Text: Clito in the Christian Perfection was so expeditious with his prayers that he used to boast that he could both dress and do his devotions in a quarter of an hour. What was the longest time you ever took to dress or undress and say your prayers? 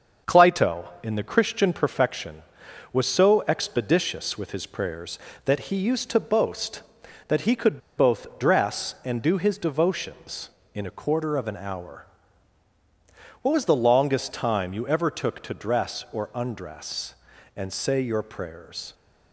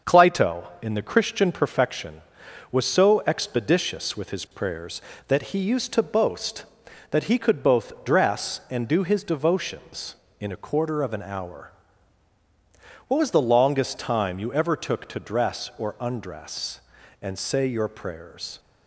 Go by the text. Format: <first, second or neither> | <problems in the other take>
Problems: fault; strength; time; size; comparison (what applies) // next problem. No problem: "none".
second | starts louder than the rest; until 1.4 s; 6.5 dB; also in the second // pauses between "could" and "both"; slight; at 7.8 s; 0.17 s long